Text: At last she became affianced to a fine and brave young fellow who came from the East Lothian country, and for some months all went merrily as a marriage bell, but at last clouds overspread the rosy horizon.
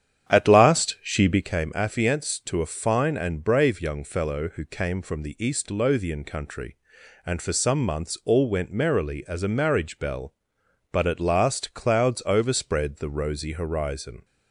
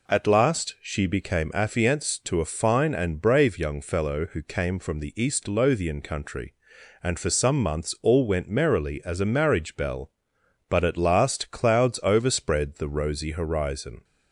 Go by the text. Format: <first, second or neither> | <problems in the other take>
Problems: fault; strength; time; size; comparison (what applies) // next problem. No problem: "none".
second | starts louder than the rest; strong; until 1.5 s; 9 dB